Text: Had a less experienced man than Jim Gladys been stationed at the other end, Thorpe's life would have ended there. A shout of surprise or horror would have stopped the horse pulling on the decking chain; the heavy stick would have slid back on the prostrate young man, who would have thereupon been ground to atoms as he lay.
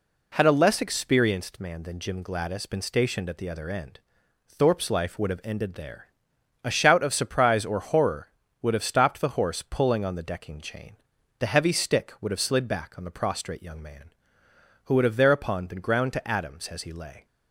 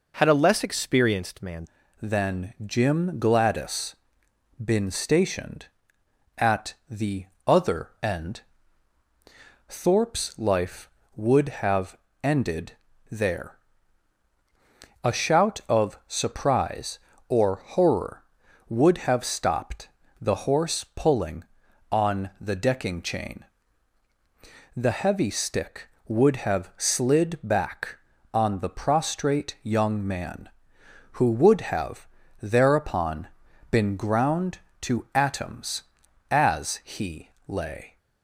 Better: first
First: none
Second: changes voice at "than"; from 2.0 s on; 35.9 s long // pauses between "Gladys" and "been"; noticeable; at 3.9 s; 0.68 s long // pauses between "at" and "the"; slight; at 6.7 s; 0.16 s long // pauses between "the" and "other"; slight; at 7.2 s; 0.22 s long // pauses between "have" and "ended"; slight; at 11.9 s; 0.24 s long // pauses between "ended" and "there"; slight; at 12.7 s; 0.36 s long // pauses between "stopped" and "the"; slight; at 19.8 s; 0.32 s long // pauses between "have" and "thereupon"; slight; at 32.0 s; 0.34 s long // pauses between "thereupon" and "been"; at 33.2 s; 0.44 s long // pauses between "he" and "lay"; slight; at 37.2 s; 0.18 s long

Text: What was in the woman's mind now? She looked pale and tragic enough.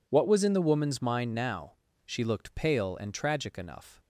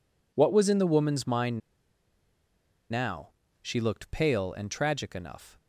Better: first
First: none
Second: pauses between "mind" and "now"; strong; at 1.6 s; 1.3 s long

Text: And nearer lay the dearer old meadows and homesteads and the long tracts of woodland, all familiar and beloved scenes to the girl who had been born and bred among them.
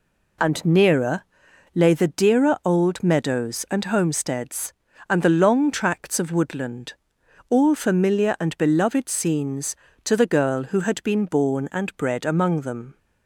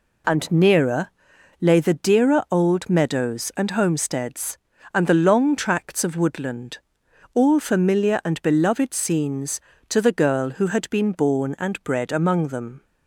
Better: neither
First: pauses between "nearer" and "lay"; noticeable; at 1.2 s; 0.52 s long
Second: pauses between "nearer" and "lay"; noticeable; at 1.0 s; 0.52 s long

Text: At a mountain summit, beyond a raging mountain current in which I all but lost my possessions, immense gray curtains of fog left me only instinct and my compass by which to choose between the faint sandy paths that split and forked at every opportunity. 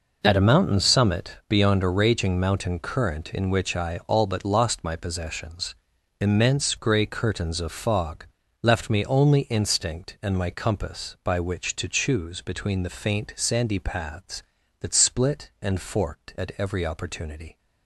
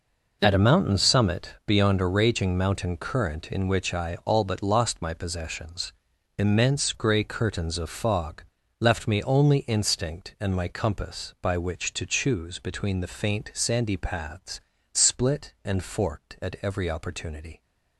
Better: first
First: pauses between "fog" and "left"; slight; at 8.2 s; 0.36 s long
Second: pauses between "fog" and "left"; slight; at 8.4 s; 0.36 s long // skips "that"; at 14.7 s

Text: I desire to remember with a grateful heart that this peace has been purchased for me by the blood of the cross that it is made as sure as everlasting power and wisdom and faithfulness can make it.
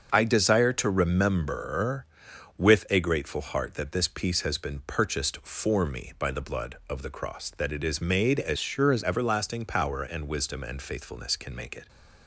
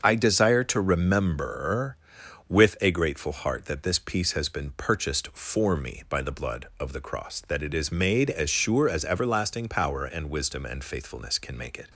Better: second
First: starts louder than the rest; until 1.1 s; 6.5 dB // changes voice from "sure" to "as"; from 8.5 to 9.0 s; 0.5 s long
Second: starts louder than the rest; until 1.0 s; 6.5 dB

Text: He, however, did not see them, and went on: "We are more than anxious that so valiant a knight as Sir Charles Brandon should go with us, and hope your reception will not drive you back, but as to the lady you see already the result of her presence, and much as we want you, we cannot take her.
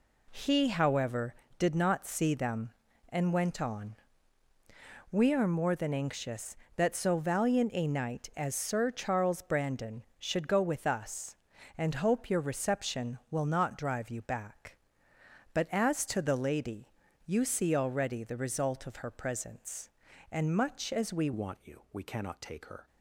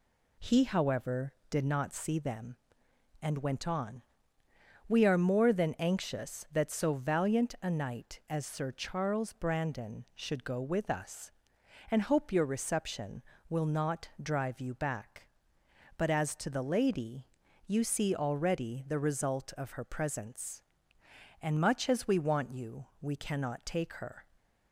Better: second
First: pauses between "lady" and "you"; slight; at 16.9 s; 0.34 s long // changes voice at "want"; from 21.3 s on; 1.5 s long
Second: pauses between "lady" and "you"; at 17.2 s; 0.40 s long

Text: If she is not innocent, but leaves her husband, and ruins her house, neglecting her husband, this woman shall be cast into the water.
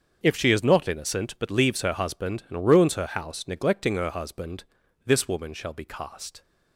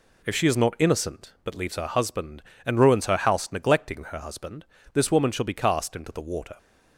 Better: second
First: starts louder than the rest; until 1.2 s; 6.5 dB // stops before "into the water"; at 6.4 s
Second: none

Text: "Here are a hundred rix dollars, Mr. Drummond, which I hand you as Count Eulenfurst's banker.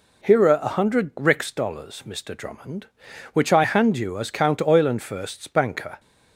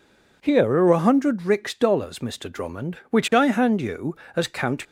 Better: first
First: none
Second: stops before "Eulenfurst's banker"; at 4.8 s

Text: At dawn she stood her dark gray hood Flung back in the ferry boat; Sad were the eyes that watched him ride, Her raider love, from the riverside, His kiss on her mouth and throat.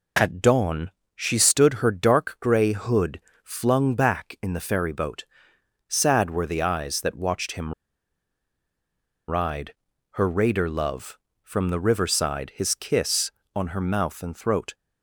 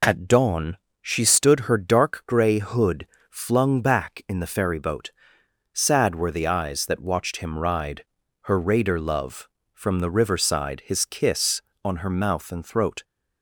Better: second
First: pauses between "dawn" and "she"; slight; at 0.8 s; 0.26 s long // pauses between "hood" and "Flung"; slight; at 3.1 s; 0.24 s long // pauses between "him" and "ride"; strong; at 7.7 s; 1.5 s long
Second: pauses between "dawn" and "she"; slight; at 0.7 s; 0.26 s long // pauses between "hood" and "Flung"; slight; at 3.0 s; 0.24 s long

